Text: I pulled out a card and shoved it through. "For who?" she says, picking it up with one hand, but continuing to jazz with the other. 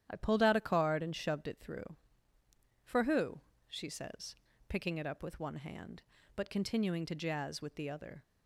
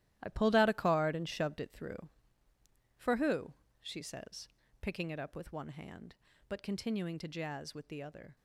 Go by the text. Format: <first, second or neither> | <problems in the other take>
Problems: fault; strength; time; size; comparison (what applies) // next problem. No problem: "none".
first | gets quieter; strong; throughout; 10 dB // starts louder than the rest; strong; until 1.2 s; 13.5 dB; strong in the first